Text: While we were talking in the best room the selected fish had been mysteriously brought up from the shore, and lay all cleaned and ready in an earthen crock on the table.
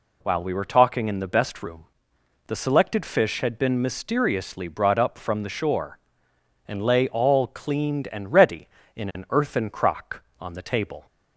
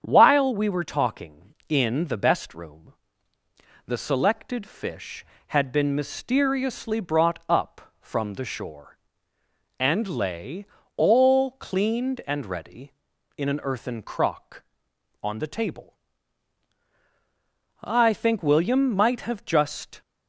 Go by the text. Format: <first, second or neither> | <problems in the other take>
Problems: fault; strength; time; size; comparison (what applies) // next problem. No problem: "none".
first | starts louder than the rest; strong; until 1.0 s; 8 dB // pauses between "room" and "the"; noticeable; at 2.9 s; 0.90 s long; noticeable in the first // pauses between "lay" and "all"; slight; at 10.6 s; 0.32 s long // goes on to say "I think William might have just"; strong; from 17.8 s on; 2.1 s long